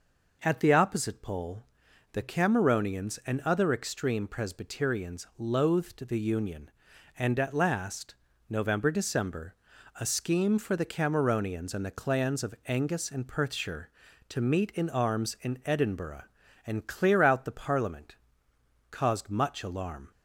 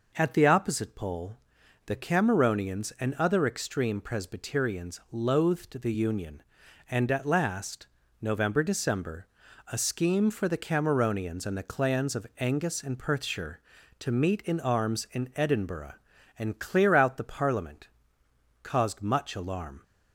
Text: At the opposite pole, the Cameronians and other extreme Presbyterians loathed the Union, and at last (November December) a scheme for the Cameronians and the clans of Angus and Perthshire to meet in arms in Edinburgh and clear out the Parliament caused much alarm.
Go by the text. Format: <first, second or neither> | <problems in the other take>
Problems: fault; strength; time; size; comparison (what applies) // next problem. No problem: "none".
neither | pauses between "Parliament" and "caused"; noticeable; the same in both